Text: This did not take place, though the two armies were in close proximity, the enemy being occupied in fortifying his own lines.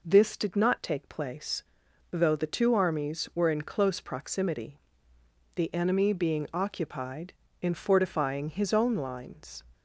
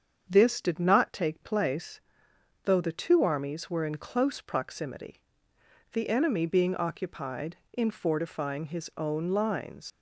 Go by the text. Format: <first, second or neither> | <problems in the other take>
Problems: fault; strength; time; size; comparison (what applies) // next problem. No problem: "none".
first | starts louder than the rest; strong; until 1.3 s; 7.5 dB // leaves "lines" unfinished; at 9.9 s; 120 ms